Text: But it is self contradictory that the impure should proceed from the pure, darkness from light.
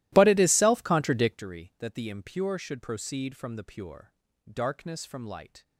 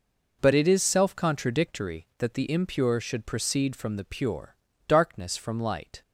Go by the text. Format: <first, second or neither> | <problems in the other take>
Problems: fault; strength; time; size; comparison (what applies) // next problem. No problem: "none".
second | starts louder than the rest; strong; until 1.5 s; 16 dB